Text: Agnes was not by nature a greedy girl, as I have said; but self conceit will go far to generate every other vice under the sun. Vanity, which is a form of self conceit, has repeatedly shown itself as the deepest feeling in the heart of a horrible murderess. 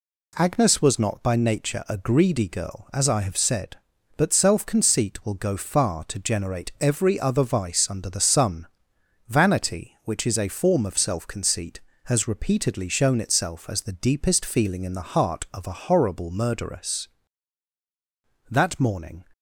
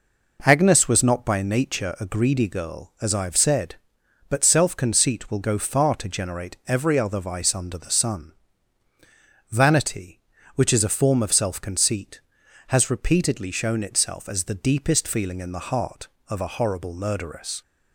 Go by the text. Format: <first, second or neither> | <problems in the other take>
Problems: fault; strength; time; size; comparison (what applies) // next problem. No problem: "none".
second | goes on to say "That morning"; noticeable; from 18.4 s on; 0.74 s long